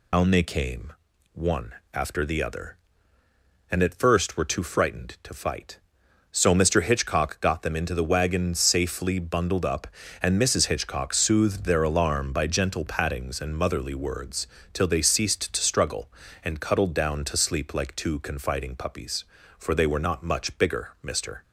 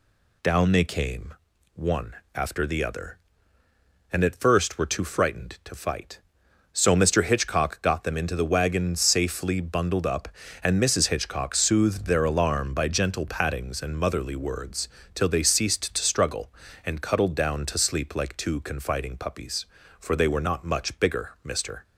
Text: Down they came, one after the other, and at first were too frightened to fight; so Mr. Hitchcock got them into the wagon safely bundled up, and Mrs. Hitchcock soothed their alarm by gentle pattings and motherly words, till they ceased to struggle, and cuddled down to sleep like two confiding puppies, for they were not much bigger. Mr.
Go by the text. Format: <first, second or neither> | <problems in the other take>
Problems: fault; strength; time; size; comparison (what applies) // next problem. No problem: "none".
second | loses the start of "Down"; at 0.1 s; 130 ms // pauses between "one" and "after"; slight; at 1.7 s; 0.18 s long; slight in the second